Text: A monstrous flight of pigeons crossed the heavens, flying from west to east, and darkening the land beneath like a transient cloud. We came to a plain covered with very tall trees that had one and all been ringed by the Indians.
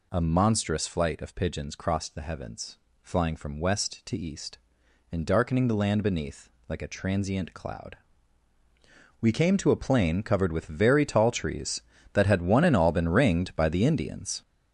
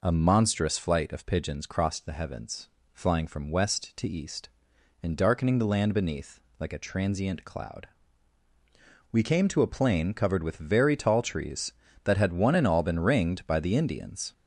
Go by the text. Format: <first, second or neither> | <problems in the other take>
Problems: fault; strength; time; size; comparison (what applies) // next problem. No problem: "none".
second | gets louder; strong; throughout; 7 dB // pauses between "beneath" and "like"; slight; at 6.4 s; 0.18 s long; slight in the second